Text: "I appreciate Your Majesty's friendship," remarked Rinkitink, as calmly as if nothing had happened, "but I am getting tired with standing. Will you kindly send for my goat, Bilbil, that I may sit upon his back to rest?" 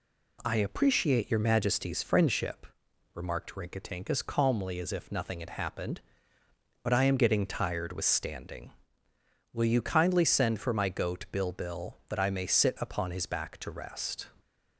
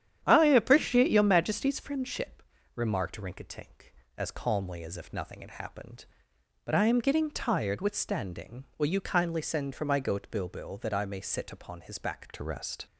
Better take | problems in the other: first | starts louder than the rest; strong; until 1.2 s; 9.5 dB // changes voice at "to"; from 12.3 s on; 0.5 s long

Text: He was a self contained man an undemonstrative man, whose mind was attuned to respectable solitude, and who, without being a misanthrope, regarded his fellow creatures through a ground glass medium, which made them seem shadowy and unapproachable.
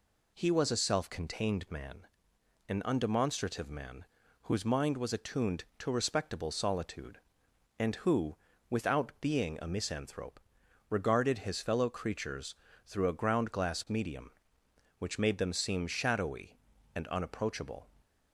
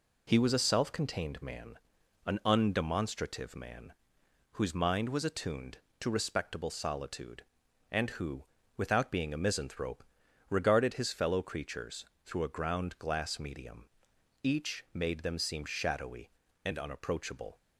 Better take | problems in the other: first | pauses between "man" and "an"; noticeable; at 1.7 s; 0.48 s long; noticeable in the first // pauses between "creatures" and "through"; slight; at 12.0 s; 0.22 s long; slight in the first // says "each" for "which"; at 14.4 s

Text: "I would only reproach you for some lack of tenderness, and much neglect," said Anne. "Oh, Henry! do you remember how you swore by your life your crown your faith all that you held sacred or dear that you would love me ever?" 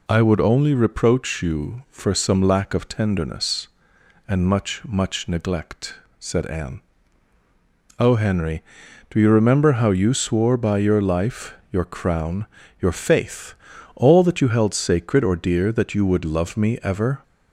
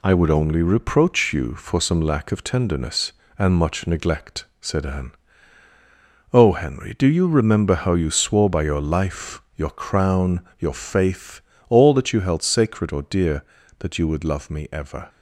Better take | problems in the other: second | says "much" twice; at 4.8 s // pauses between "life" and "your"; slight; at 11.5 s; 0.18 s long // pauses between "crown" and "your"; slight; at 12.4 s; 0.34 s long; slight in the second // pauses between "faith" and "all"; at 13.5 s; 0.42 s long; slight in the second

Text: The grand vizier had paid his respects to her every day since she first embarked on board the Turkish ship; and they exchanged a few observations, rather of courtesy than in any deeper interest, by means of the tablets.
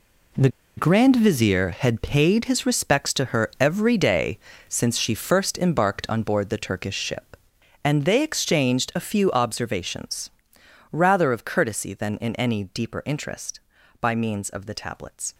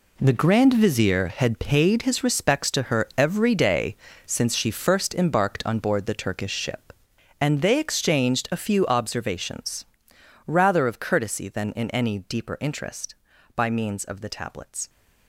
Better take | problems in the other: second | pauses between "The" and "grand"; slight; at 0.4 s; 0.28 s long // pauses between "day" and "since"; slight; at 4.4 s; 0.28 s long; slight in the second

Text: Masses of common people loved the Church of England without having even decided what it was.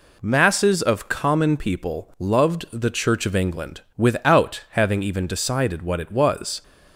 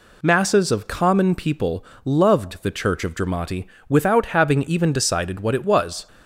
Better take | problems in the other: first | pauses between "people" and "loved"; slight; at 1.8 s; 0.18 s long // says "Dramati" for "England"; at 3.1 s

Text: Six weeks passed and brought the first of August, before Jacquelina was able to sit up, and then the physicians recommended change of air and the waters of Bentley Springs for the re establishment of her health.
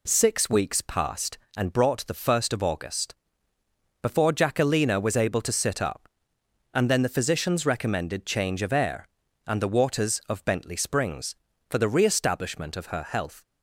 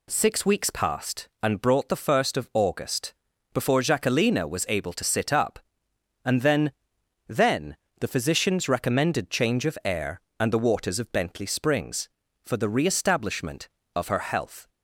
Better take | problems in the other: first | says "then" twice; at 7.2 s

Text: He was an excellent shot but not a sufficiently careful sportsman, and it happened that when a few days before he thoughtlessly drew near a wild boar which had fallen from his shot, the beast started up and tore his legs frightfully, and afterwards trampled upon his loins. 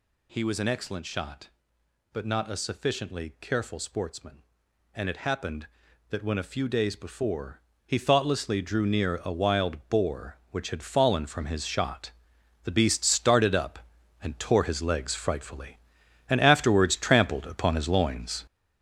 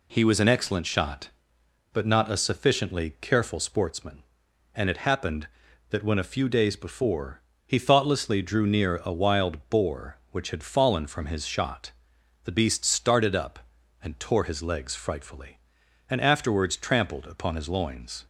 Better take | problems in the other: second | gets louder; throughout; 7 dB // pauses between "before" and "he"; slight; at 7.5 s; 0.26 s long; slight in the second

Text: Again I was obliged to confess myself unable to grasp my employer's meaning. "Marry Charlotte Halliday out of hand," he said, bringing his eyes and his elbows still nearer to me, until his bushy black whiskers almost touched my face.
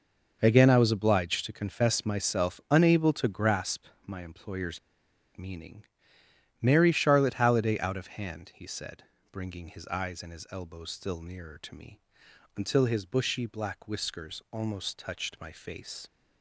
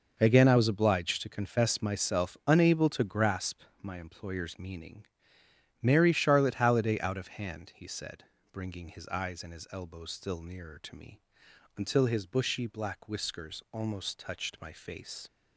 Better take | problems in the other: second | pauses between "grasp" and "my"; slight; at 3.8 s; 0.20 s long; slight in the second // pauses between "employer's" and "meaning"; noticeable; at 4.7 s; 0.56 s long

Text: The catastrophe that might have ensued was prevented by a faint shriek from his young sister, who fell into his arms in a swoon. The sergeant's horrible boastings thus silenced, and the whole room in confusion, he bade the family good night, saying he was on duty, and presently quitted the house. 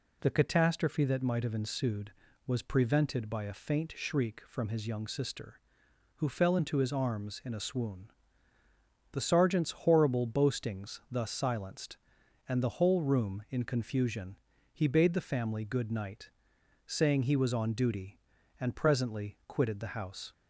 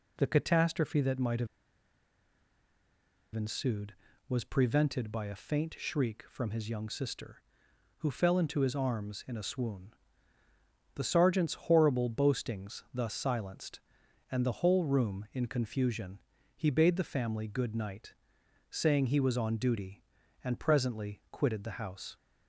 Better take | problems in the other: first | pauses between "have" and "ensued"; strong; at 1.4 s; 1.8 s long

